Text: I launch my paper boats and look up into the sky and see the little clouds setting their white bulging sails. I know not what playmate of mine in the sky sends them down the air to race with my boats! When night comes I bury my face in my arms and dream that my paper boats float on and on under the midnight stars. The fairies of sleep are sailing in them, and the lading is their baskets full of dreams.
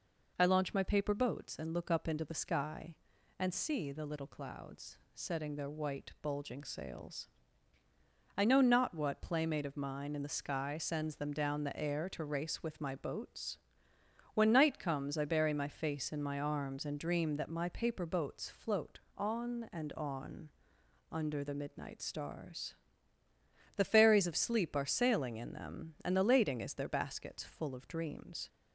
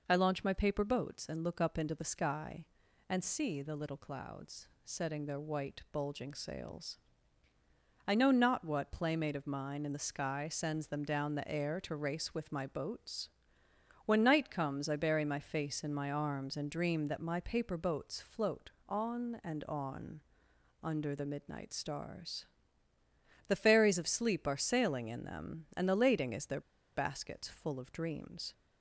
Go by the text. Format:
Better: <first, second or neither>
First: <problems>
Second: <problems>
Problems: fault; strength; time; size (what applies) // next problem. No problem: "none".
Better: first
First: pauses between "clouds" and "setting"; slight; at 4.9 s; 0.16 s long // pauses between "on" and "under"; noticeable; at 20.4 s; 0.62 s long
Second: pauses between "clouds" and "setting"; slight; at 4.6 s; 0.16 s long // pauses between "on" and "under"; noticeable; at 20.2 s; 0.62 s long // pauses between "their" and "baskets"; slight; at 26.6 s; 0.35 s long